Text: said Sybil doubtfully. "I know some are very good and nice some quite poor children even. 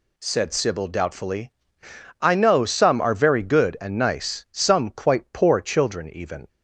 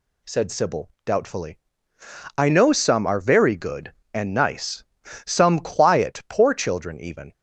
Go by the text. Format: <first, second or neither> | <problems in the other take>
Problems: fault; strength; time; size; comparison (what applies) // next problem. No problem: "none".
first | pauses between "nice" and "some"; at 4.8 s; 0.40 s long // says "quiet" for "quite"; at 5.5 s